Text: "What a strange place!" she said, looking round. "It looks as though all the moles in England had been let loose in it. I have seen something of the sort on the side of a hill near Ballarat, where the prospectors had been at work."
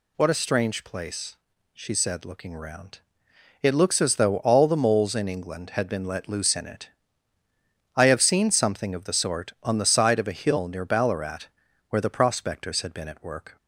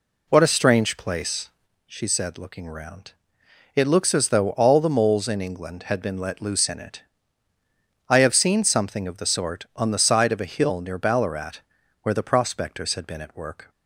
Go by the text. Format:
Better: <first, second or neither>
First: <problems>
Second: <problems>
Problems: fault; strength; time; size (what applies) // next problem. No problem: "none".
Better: first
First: none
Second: starts louder than the rest; slight; until 1.7 s; 2.5 dB